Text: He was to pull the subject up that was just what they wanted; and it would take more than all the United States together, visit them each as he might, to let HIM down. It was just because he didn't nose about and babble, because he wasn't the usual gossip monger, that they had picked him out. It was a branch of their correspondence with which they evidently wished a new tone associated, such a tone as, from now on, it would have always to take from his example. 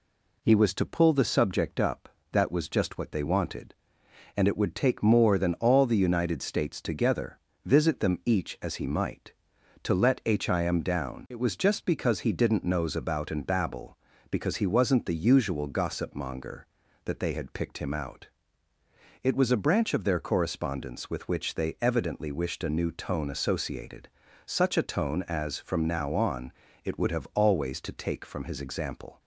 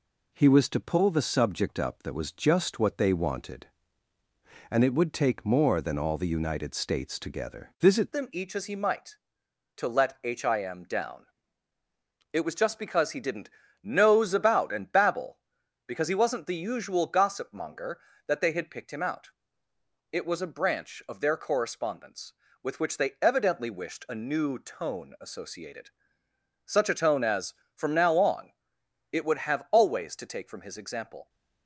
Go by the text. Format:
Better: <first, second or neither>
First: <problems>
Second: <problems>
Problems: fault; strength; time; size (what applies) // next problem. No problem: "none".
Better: first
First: none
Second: changes voice at "them"; from 8.1 s on; 23.1 s long // pauses between "didn't" and "nose"; slight; at 13.4 s; 0.34 s long